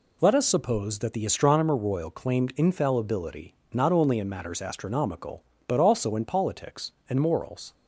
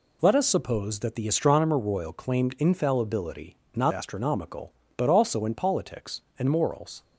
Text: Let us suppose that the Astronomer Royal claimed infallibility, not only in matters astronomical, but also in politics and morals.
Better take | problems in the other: first | skips "only in matters"; at 3.9 s

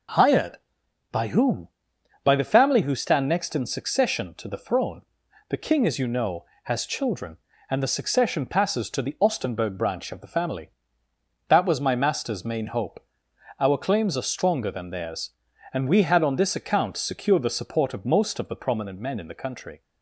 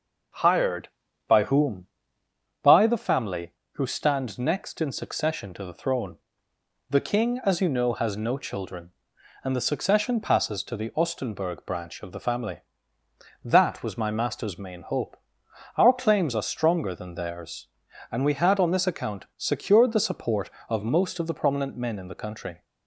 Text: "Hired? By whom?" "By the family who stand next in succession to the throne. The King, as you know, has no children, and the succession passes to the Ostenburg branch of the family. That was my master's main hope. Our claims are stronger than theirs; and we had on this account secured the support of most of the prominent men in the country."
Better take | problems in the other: second | skips "no"; at 6.8 s

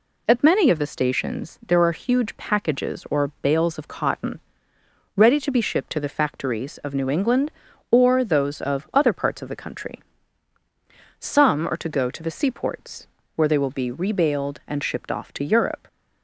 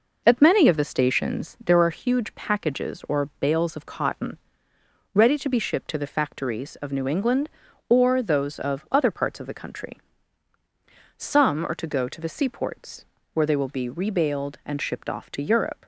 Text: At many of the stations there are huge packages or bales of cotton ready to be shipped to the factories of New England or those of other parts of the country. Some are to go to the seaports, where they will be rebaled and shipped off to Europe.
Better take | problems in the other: first | starts louder than the rest; noticeable; until 2.0 s; 5 dB // pauses between "cotton" and "ready"; noticeable; at 4.3 s; 0.76 s long; noticeable in the first

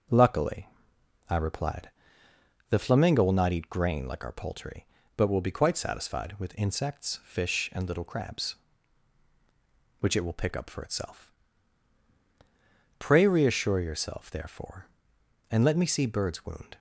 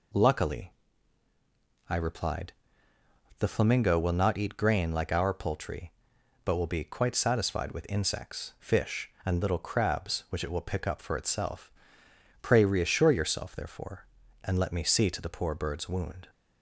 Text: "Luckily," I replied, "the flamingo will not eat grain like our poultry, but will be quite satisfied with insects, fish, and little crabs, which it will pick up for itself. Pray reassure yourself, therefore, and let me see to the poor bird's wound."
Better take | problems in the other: second | starts louder than the rest; until 1.7 s; 6.5 dB // skips "to the poor"; at 16.0 s

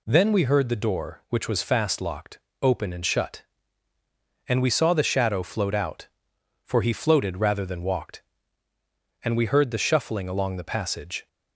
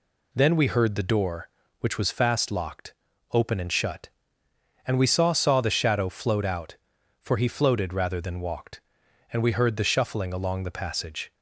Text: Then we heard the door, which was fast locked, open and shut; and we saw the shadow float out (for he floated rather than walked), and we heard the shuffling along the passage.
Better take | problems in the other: first | says "saw" twice; at 5.3 s

